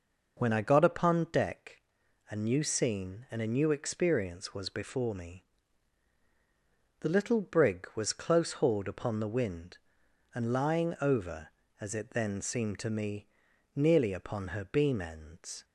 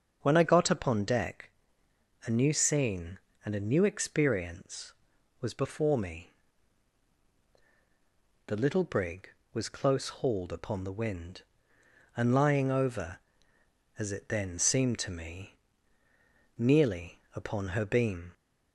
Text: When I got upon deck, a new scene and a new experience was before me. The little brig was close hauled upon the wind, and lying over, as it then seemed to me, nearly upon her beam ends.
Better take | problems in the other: first | starts louder than the rest; until 1.2 s; 6.5 dB // stops before "ends"; at 18.3 s

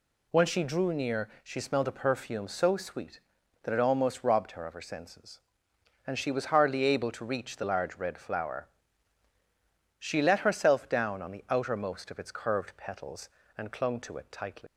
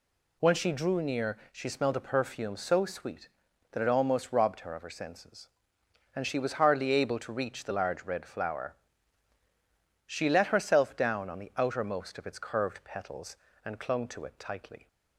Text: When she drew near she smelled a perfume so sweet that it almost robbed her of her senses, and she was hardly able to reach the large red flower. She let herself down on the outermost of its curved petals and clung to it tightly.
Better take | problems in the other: second | pauses between "near" and "she"; slight; at 1.2 s; 0.16 s long; slight in the second // leaves "tightly" unfinished; at 14.6 s; 130 ms

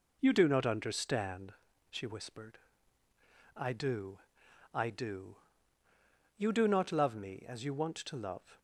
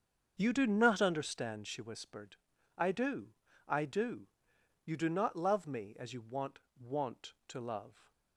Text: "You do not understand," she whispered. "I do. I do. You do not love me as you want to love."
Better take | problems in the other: first | starts louder than the rest; until 1.3 s; 7 dB // says "want" twice; at 6.7 s

